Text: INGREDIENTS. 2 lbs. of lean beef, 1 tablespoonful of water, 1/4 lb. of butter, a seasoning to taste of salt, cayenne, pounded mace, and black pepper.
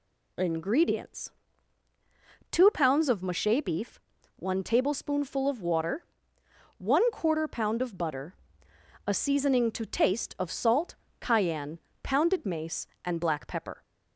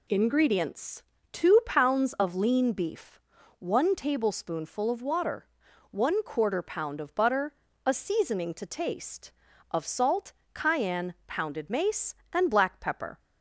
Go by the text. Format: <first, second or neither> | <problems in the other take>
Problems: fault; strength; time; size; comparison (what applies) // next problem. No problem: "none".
second | says "mache" for "lean"; at 3.2 s